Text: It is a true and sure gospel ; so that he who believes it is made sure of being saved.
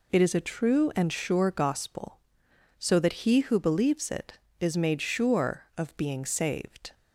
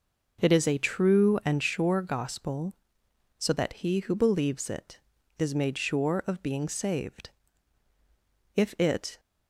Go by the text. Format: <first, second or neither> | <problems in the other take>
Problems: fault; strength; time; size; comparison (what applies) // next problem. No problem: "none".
first | goes on to say "If it"; noticeable; from 8.5 s on; 0.64 s long